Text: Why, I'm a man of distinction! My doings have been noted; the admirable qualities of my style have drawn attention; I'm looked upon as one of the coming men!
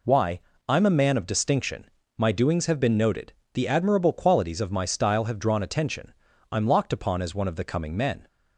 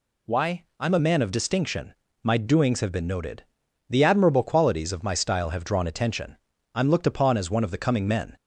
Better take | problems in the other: second | says "locked" for "looked"; at 6.6 s

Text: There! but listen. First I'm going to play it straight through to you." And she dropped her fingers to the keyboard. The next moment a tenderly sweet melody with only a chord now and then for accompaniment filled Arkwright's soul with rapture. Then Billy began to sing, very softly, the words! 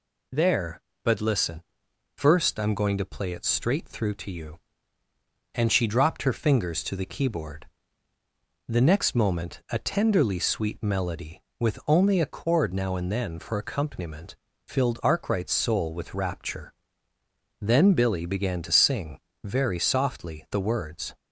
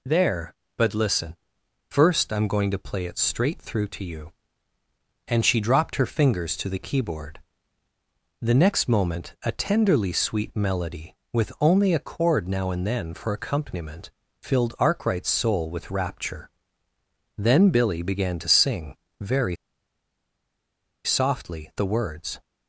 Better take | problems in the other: first | pauses between "accompaniment" and "filled"; slight; at 14.1 s; 0.30 s long; slight in the first // pauses between "very" and "softly"; strong; at 19.5 s; 1.5 s long

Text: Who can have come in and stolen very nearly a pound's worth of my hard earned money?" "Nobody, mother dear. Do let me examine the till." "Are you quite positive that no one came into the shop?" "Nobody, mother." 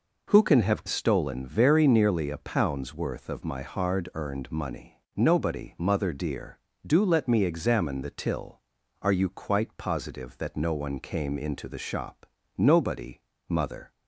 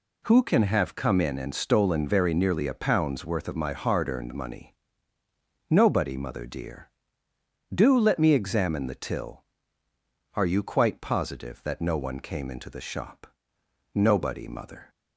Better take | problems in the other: second | skips "come in and"; at 0.8 s

